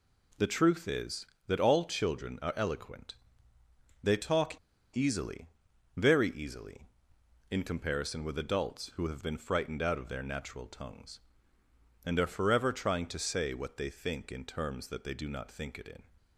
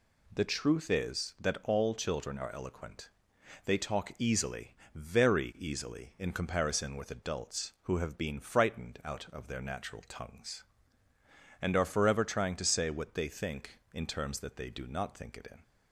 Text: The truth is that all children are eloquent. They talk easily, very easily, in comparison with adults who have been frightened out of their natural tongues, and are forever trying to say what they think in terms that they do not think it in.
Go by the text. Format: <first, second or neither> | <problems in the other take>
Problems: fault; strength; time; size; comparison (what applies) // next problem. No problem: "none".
second | pauses between "talk" and "easily"; at 4.5 s; 0.36 s long